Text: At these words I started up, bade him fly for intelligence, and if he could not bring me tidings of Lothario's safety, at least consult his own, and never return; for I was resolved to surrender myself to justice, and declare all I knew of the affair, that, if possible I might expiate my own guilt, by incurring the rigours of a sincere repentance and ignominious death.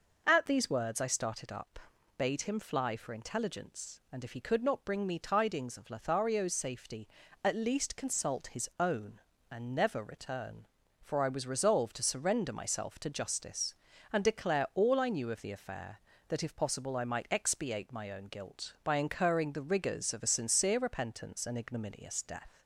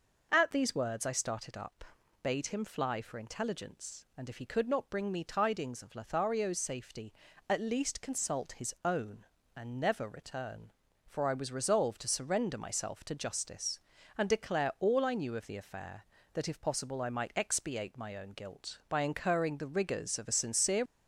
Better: first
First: none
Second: stops before "repentance and ignominious death"; at 20.8 s

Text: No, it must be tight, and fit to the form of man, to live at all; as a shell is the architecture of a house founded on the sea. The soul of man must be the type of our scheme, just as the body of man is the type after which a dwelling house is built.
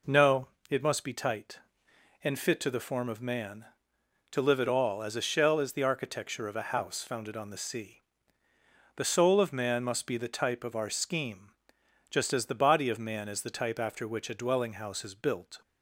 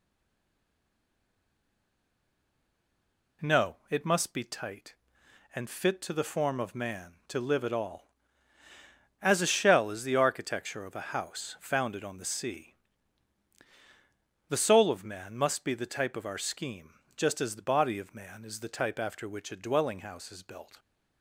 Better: first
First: none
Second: stays silent before the first word; strong; until 3.4 s; 3.4 s long

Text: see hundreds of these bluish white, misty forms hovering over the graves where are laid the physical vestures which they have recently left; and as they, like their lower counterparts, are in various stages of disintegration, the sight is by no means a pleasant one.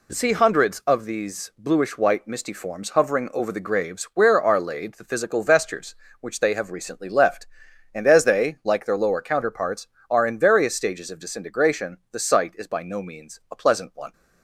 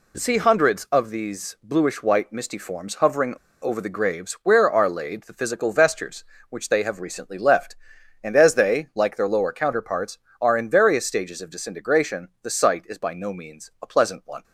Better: first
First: none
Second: pauses between "hovering" and "over"; slight; at 3.3 s; 0.27 s long

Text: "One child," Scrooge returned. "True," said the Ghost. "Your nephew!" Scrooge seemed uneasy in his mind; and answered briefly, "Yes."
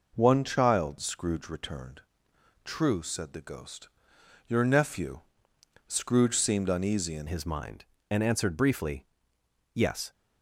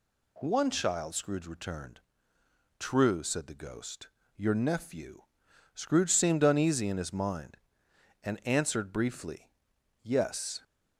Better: second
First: changes voice at "his"; from 7.2 s on; 2.9 s long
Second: none

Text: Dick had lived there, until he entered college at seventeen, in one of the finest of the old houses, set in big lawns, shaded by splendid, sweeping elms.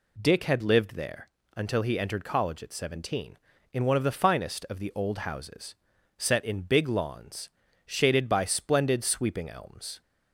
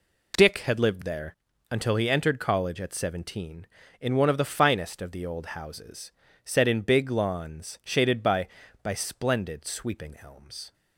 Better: first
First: none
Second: says "by" twice; at 8.8 s

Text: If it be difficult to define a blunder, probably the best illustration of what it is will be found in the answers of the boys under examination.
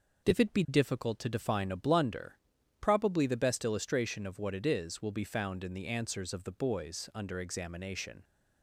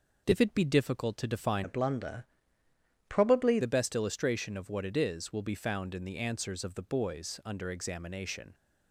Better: first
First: none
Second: changes voice from "a" to "probably"; from 1.6 to 3.5 s; 1.9 s long

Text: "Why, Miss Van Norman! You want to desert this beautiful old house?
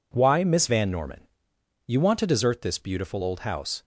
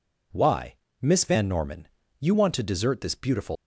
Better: first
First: none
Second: stops before "old house"; at 3.5 s

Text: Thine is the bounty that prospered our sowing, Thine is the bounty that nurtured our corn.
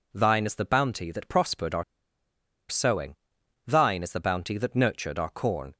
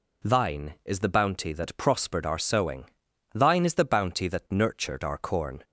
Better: second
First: pauses between "our" and "sowing"; noticeable; at 1.8 s; 0.85 s long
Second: none

